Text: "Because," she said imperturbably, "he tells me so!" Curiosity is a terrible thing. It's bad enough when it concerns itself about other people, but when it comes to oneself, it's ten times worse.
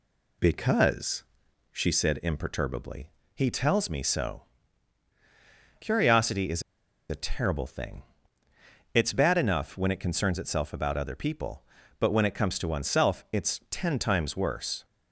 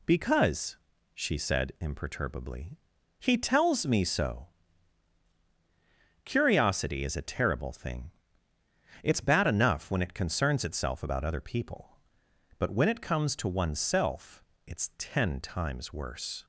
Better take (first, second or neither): second